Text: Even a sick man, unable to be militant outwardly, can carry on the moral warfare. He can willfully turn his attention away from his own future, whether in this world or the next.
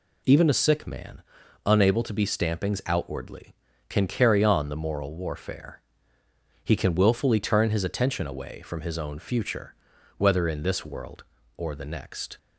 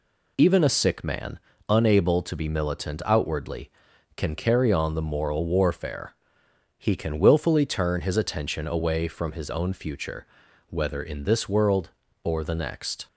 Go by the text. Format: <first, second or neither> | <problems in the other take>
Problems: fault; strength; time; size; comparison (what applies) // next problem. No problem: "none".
second | says "stampings" for "militant"; at 2.2 s